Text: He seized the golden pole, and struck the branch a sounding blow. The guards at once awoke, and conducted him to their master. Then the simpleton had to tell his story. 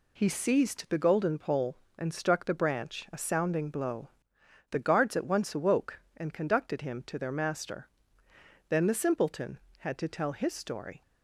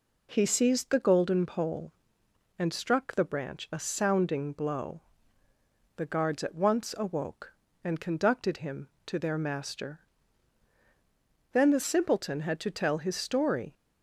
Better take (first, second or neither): neither